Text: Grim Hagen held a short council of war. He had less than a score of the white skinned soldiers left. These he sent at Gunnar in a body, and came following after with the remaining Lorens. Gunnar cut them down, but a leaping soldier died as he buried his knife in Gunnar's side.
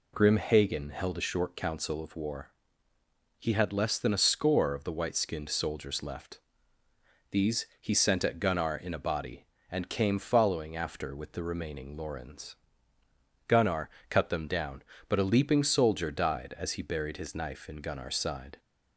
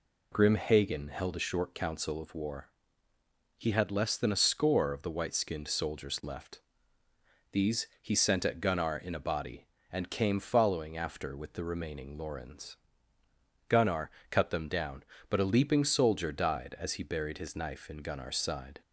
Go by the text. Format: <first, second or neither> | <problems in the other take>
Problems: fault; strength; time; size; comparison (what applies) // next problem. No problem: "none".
neither | pauses between "Gunnar" and "cut"; slight; the same in both